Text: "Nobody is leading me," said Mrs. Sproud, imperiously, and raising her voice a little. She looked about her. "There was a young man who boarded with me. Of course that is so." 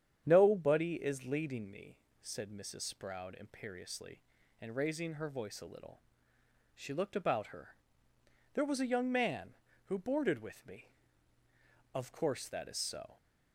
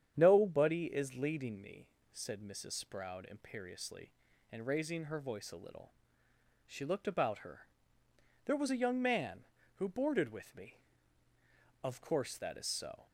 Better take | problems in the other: neither | starts louder than the rest; strong; the same in both

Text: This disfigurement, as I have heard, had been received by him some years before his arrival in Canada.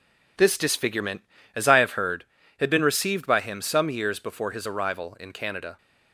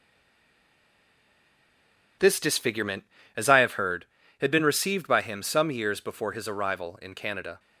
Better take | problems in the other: first | stays silent before the first word; until 2.2 s; 2.2 s long

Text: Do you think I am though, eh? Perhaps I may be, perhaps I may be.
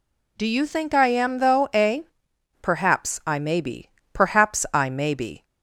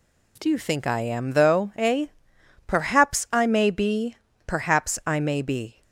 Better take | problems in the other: neither | none

